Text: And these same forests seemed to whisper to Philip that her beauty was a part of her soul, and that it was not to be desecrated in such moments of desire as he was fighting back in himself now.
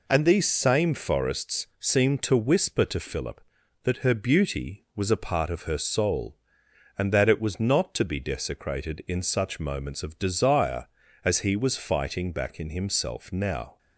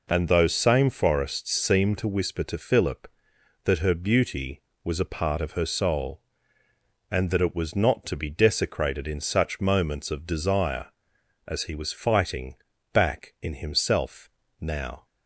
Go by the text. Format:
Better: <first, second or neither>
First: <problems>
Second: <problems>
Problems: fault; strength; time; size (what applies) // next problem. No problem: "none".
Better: first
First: none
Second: says "those" for "these"; at 0.2 s // pauses between "fighting" and "back"; at 12.5 s; 0.38 s long // pauses between "himself" and "now"; slight; at 14.3 s; 0.30 s long